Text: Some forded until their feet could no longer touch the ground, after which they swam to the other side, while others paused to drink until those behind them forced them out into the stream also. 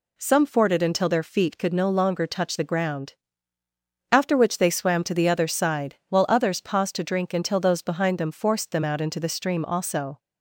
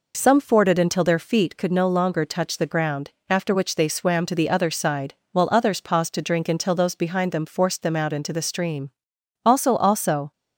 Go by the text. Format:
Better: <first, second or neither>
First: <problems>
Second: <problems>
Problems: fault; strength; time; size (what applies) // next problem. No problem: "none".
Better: first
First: none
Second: pauses between "stream" and "also"; noticeable; at 8.9 s; 0.52 s long // says "also" twice; at 9.7 s